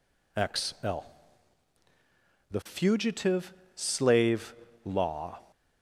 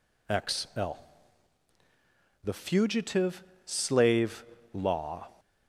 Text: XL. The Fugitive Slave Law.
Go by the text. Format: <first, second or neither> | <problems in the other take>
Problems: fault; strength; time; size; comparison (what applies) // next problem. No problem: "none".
neither | pauses between "Fugitive" and "Slave"; slight; the same in both // pauses between "Slave" and "Law"; slight; the same in both